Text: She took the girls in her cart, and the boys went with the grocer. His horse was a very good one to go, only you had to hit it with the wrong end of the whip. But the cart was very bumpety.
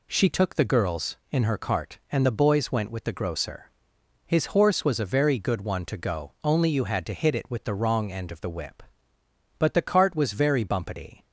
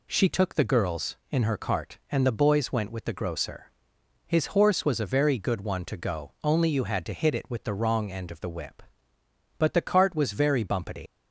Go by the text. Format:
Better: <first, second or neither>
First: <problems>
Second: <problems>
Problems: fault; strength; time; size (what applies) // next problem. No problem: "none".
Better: first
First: none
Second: leaves "bumpety" unfinished; at 11.0 s; 180 ms